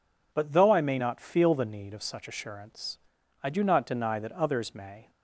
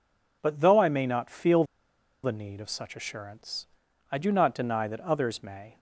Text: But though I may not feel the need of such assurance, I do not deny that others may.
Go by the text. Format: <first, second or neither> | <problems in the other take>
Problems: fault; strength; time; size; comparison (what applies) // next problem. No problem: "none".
first | pauses between "feel" and "the"; noticeable; at 1.6 s; 0.60 s long